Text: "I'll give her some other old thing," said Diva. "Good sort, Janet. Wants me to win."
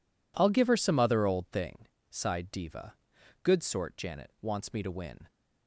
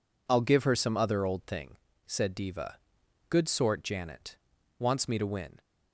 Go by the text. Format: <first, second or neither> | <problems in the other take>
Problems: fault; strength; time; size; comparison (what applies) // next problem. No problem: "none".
second | says "sighed" for "said"; at 2.0 s